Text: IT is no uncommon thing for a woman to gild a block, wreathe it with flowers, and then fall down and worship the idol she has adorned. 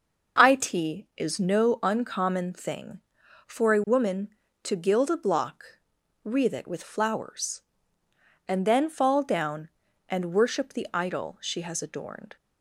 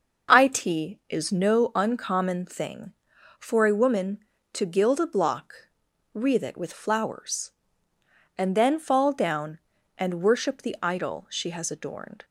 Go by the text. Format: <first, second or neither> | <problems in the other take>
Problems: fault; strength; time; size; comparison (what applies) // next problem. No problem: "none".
neither | none